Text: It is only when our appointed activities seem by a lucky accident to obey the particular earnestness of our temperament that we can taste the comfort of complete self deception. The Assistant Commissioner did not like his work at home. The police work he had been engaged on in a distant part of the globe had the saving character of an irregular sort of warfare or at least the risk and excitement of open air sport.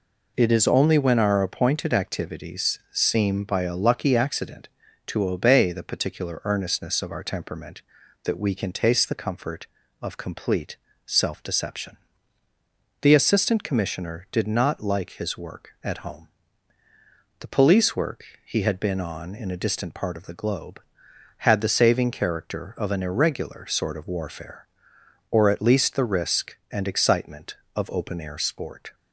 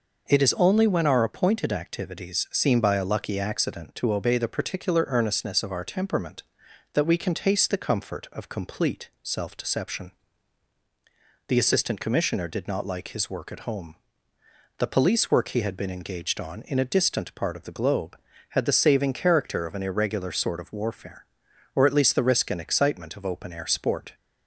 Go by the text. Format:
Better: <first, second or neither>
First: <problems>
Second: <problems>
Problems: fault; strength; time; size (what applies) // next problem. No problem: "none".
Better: second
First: pauses between "complete" and "self"; slight; at 10.7 s; 0.30 s long // pauses between "work" and "he"; slight; at 18.2 s; 0.20 s long // skips "engaged"; at 18.9 s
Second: none